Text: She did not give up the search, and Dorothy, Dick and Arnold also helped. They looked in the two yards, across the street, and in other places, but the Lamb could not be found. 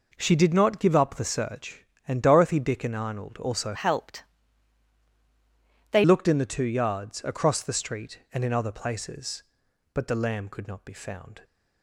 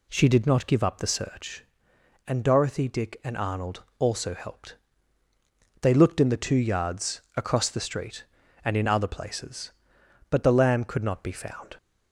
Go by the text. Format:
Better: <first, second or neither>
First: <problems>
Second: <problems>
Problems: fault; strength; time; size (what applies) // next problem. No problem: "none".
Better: second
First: changes voice from "helped" to "They"; from 3.7 to 6.0 s; 2.3 s long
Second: none